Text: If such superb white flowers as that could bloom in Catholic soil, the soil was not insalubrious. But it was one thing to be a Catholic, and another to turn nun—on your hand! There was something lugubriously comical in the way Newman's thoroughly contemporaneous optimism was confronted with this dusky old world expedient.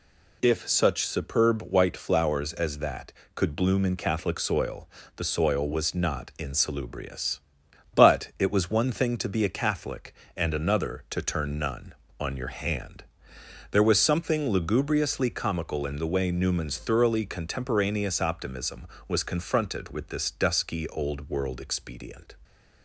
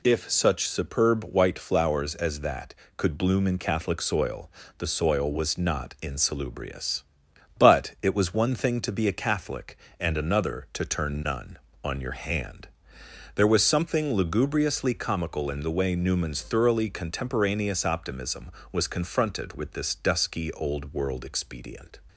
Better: neither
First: none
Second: none

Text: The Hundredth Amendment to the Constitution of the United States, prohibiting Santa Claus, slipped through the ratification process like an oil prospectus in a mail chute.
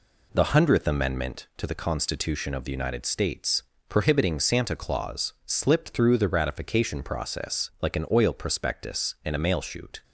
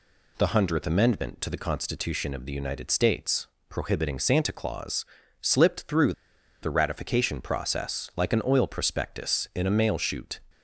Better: first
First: none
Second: pauses between "through" and "the"; noticeable; at 6.1 s; 0.50 s long

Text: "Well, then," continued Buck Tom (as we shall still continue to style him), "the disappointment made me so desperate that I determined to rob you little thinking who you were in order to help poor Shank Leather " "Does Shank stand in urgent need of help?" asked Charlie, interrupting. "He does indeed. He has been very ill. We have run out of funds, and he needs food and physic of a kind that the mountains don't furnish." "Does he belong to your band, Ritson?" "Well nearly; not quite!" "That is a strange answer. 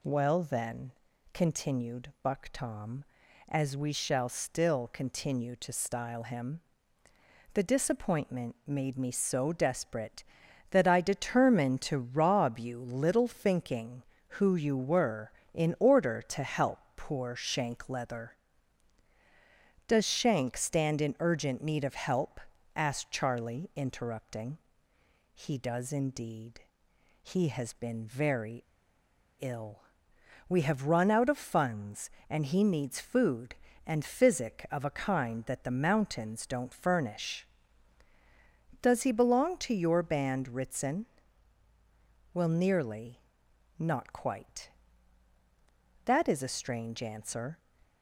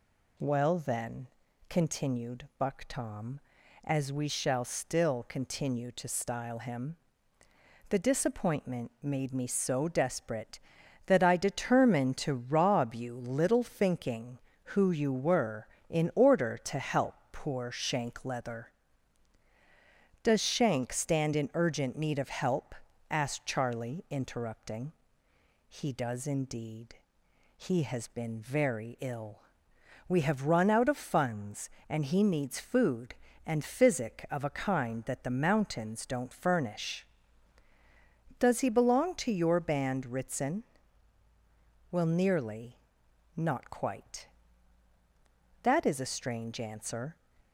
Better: second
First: pauses between "help" and "poor"; slight; at 16.7 s; 0.16 s long // pauses between "very" and "ill"; noticeable; at 28.6 s; 0.79 s long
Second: pauses between "help" and "poor"; slight; at 17.1 s; 0.16 s long

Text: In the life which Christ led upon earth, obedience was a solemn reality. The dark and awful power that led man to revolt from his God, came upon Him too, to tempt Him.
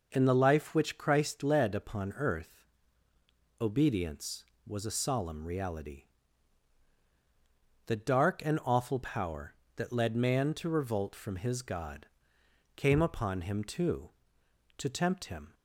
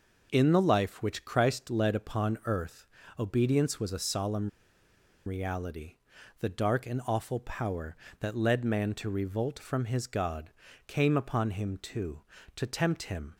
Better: first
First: none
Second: pauses between "solemn" and "reality"; noticeable; at 4.4 s; 0.78 s long

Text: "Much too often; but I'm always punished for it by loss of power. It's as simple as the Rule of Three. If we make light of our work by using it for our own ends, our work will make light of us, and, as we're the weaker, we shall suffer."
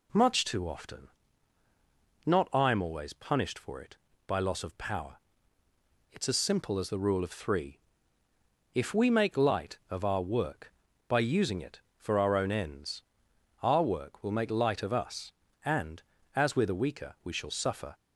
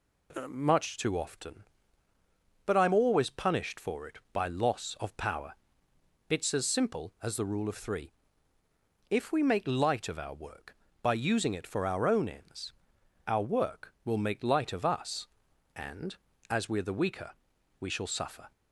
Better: second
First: says "not" for "but"; at 2.2 s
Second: none

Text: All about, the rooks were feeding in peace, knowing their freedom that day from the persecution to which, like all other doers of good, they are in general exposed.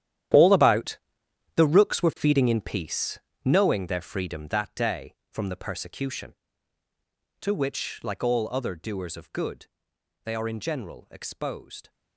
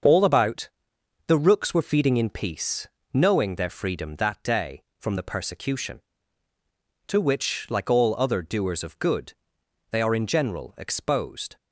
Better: second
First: gets quieter; strong; throughout; 15 dB // starts louder than the rest; strong; until 1.9 s; 11.5 dB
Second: starts louder than the rest; until 1.6 s; 6.5 dB

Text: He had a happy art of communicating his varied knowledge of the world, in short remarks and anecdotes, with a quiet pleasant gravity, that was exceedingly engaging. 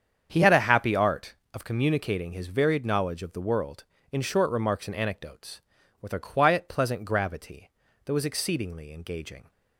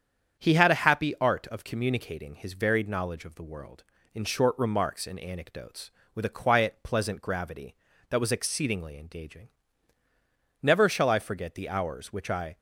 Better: first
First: starts louder than the rest; strong; until 1.3 s; 7.5 dB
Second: starts louder than the rest; strong; until 1.4 s; 8 dB // goes on to say "Never shall I forget the hours which I"; strong; from 10.6 s on; 1.9 s long

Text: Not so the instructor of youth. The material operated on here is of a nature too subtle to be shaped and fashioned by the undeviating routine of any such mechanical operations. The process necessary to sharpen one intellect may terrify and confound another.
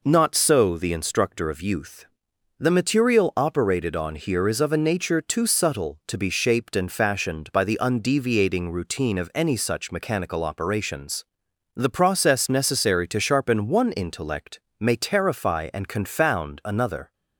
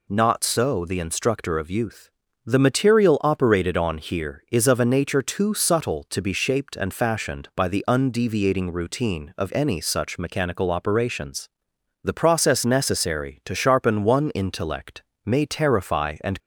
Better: first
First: pauses between "intellect" and "may"; slight; at 14.5 s; 0.22 s long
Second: pauses between "intellect" and "may"; slight; at 15.0 s; 0.22 s long // stops before "confound another"; at 16.3 s

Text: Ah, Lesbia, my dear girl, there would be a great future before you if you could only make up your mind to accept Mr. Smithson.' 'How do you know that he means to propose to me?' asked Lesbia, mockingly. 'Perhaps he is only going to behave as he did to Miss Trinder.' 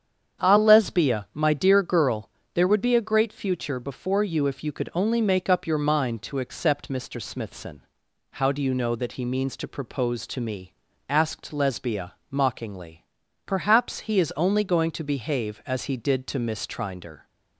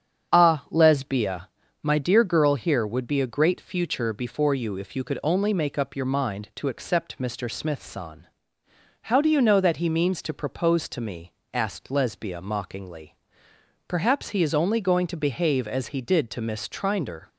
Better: first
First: starts louder than the rest; strong; until 1.5 s; 8 dB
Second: starts louder than the rest; strong; until 1.3 s; 8 dB // says "here" for "there"; at 2.5 s

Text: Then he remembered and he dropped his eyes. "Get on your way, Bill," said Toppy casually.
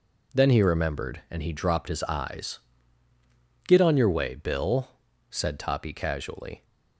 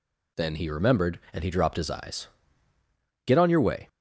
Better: first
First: none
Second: stops before "Bill said Toppy casually"; at 3.8 s

